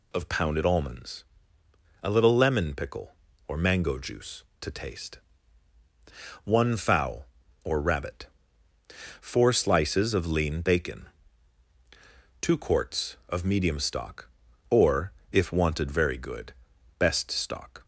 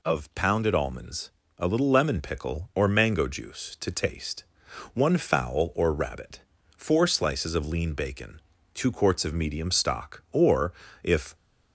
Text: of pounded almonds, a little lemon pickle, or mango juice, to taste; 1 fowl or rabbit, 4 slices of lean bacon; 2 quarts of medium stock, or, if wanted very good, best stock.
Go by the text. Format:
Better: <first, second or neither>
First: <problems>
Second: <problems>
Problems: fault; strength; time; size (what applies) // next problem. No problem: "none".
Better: first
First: none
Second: stops before "wanted very good best stock"; at 11.3 s